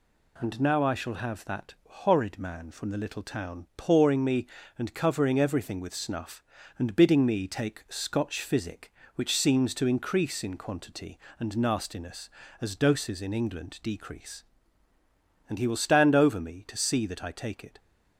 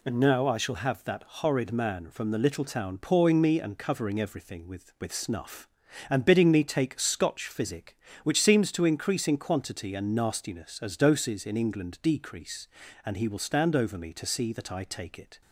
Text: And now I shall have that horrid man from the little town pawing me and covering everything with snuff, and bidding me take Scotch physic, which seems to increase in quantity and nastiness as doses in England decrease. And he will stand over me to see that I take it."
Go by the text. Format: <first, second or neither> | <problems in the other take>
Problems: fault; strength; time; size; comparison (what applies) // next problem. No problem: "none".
first | says "with" twice; at 4.9 s